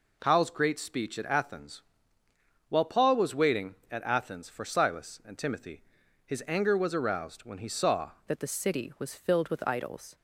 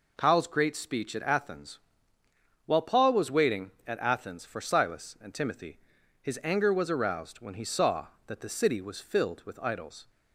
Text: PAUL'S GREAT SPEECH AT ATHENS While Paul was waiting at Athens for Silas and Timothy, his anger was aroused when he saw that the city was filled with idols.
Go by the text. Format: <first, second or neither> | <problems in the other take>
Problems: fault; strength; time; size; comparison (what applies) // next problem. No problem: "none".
second | pauses between "ATHENS" and "While"; noticeable; at 1.8 s; 0.88 s long; noticeable in the second // changes voice at "that"; from 8.2 s on; 1.9 s long